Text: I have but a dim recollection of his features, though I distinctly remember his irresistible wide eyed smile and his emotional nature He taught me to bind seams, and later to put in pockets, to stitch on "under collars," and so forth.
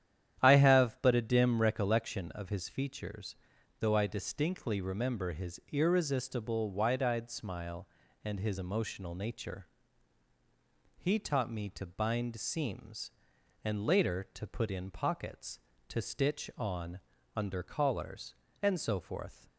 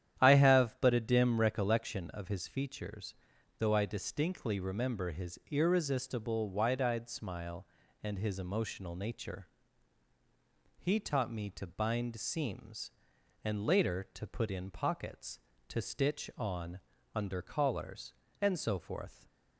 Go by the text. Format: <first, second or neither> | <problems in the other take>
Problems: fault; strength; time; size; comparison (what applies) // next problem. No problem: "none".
neither | starts louder than the rest; strong; the same in both // pauses between "nature" and "He"; strong; the same in both // pauses between "on" and "under"; slight; the same in both